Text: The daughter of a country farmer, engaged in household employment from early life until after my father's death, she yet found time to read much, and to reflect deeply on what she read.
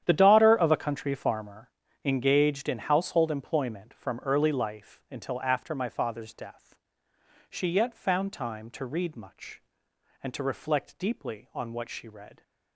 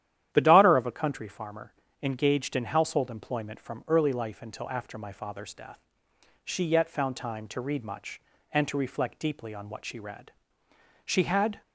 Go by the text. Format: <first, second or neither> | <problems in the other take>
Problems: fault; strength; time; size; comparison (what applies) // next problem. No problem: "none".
first | starts louder than the rest; strong; until 1.3 s; 11 dB; strong in the first // goes on to say "She had"; from 11.0 s on; 0.58 s long